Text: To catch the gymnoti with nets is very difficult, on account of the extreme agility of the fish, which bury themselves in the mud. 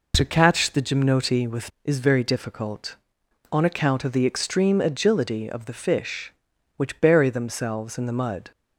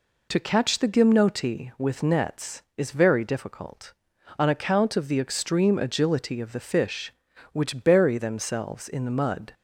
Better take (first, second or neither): second